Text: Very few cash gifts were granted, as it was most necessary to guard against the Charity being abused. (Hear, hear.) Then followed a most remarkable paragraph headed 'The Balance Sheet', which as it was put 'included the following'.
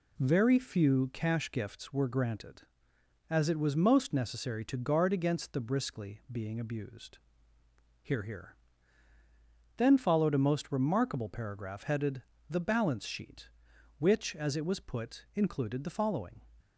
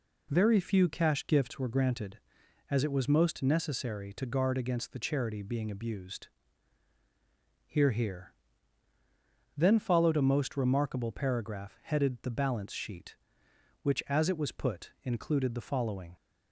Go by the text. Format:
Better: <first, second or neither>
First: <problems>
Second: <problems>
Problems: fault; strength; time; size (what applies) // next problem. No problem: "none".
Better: second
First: says "Briskly" for "Charity"; at 5.6 s // pauses between "headed" and "The"; slight; at 12.2 s; 0.26 s long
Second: none